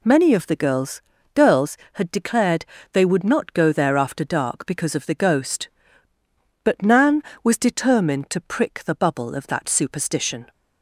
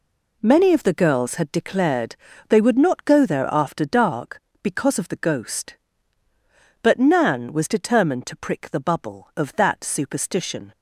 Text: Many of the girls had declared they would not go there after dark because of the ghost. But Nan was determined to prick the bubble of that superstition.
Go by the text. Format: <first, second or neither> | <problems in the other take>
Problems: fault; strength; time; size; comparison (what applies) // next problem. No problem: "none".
second | says "girls" twice; at 1.3 s // pauses between "declared" and "they"; slight; at 2.6 s; 0.28 s long; slight in the second